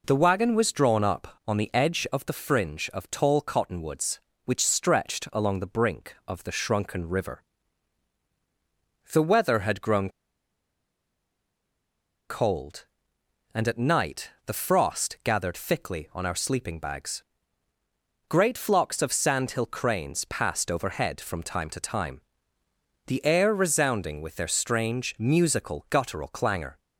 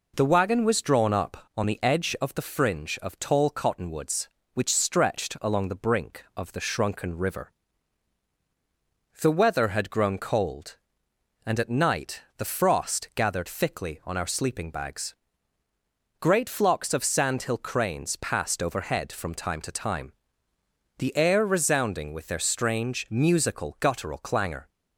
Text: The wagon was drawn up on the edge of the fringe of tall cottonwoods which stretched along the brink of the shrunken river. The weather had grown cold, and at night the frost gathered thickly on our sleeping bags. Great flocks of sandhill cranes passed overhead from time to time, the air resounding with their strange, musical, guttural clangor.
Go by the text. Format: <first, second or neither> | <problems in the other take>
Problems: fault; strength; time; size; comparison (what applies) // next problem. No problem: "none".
second | pauses between "grown" and "cold"; strong; at 10.0 s; 2.1 s long // pauses between "night" and "the"; slight; at 14.3 s; 0.16 s long; slight in the second